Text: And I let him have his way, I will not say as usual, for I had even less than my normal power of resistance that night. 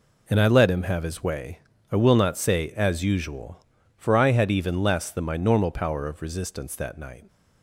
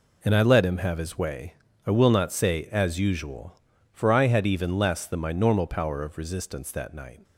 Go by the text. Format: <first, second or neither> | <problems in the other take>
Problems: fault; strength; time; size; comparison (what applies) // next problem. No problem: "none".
neither | none